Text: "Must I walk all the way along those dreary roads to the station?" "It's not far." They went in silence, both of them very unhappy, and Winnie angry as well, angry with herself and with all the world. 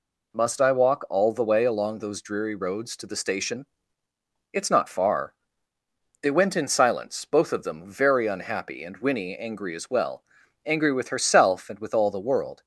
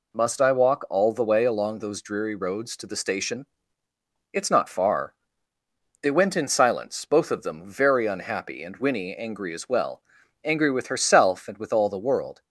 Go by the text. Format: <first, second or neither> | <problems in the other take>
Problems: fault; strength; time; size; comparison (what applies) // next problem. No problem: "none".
neither | none